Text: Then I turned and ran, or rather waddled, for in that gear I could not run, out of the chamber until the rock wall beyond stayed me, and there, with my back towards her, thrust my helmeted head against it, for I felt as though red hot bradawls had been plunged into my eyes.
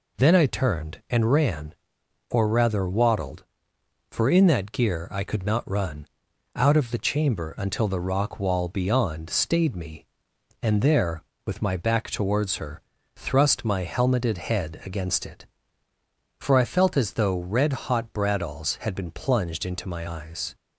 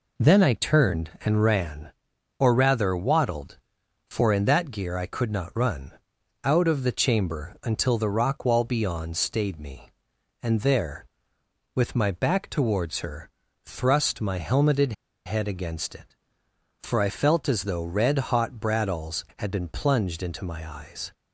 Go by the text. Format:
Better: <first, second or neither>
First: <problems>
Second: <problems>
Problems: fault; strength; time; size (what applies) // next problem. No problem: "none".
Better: first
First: none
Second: pauses between "helmeted" and "head"; slight; at 14.9 s; 0.33 s long